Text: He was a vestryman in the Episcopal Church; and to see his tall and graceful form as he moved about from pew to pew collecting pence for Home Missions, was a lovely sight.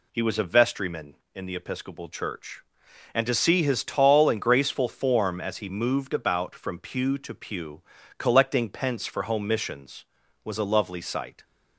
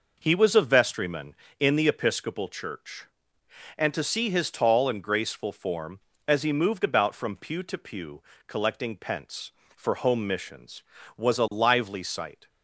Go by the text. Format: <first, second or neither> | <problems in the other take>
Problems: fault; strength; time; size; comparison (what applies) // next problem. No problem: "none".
first | pauses between "pew" and "collecting"; slight; at 8.2 s; 0.24 s long; slight in the first // says "lively" for "lovely"; at 11.5 s